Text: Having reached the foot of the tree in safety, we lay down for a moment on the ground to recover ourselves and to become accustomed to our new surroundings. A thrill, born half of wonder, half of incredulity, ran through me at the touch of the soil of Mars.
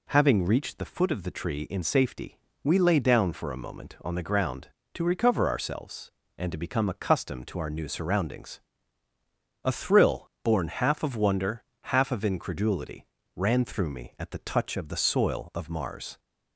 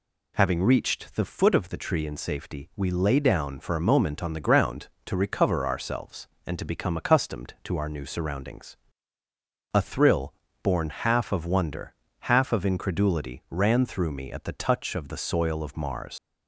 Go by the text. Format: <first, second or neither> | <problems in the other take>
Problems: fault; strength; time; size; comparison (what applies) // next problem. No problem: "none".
first | leaves "Mars" unfinished; at 16.1 s; 65 ms